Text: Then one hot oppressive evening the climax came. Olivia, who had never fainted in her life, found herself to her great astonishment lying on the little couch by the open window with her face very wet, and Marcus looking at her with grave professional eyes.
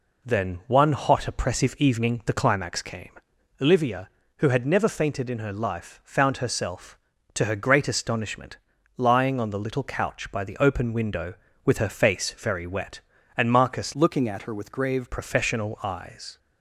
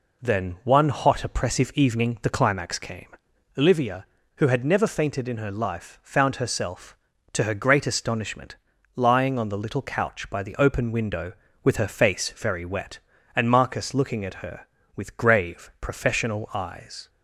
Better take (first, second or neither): second